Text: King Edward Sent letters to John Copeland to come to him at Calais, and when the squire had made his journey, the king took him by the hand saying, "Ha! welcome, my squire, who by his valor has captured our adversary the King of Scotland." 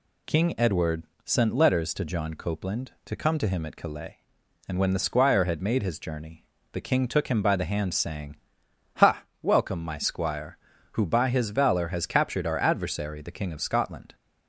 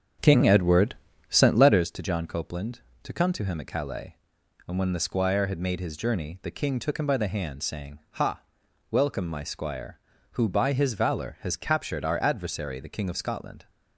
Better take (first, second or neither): first